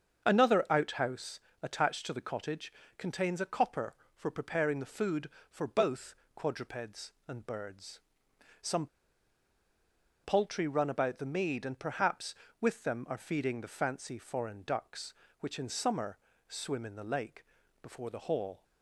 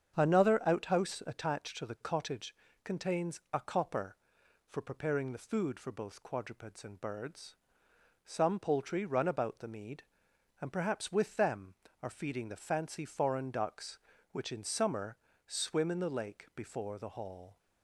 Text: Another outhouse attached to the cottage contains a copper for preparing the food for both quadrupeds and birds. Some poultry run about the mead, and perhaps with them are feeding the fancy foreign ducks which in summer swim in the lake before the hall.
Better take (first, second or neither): second